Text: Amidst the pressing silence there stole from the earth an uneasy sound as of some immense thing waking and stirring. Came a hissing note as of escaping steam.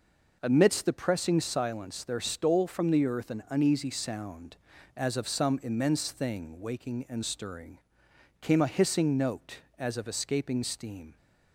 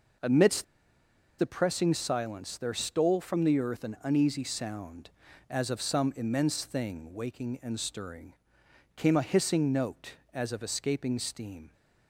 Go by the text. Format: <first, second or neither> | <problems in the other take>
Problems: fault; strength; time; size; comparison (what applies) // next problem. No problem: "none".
first | pauses between "Amidst" and "the"; noticeable; at 0.6 s; 0.73 s long